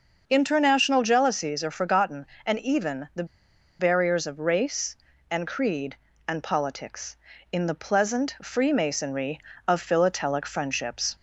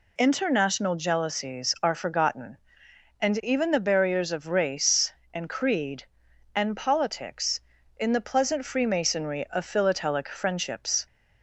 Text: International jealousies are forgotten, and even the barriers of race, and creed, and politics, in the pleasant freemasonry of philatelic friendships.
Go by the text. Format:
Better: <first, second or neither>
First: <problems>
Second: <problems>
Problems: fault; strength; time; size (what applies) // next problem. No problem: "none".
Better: second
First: starts louder than the rest; until 1.2 s; 6 dB // pauses between "the" and "barriers"; noticeable; at 3.2 s; 0.56 s long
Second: none